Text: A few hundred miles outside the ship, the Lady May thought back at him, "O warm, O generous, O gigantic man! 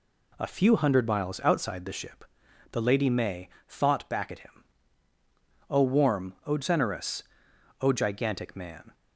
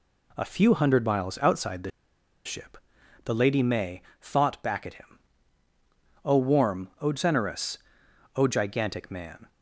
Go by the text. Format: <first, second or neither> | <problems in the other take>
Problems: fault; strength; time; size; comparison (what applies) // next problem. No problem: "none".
first | pauses between "the" and "ship"; noticeable; at 1.8 s; 0.56 s long // pauses between "May" and "thought"; slight; at 4.0 s; 0.18 s long; slight in the first